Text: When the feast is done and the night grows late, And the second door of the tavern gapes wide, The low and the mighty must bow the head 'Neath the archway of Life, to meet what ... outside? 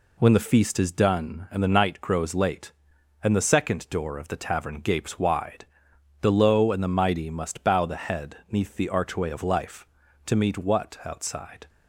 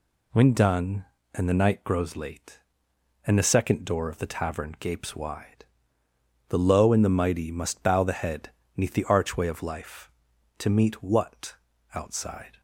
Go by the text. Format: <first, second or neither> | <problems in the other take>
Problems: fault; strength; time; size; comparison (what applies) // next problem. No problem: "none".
first | skips "the feast is"; at 0.5 s // pauses between "head" and "Neath"; slight; at 8.5 s; 0.26 s long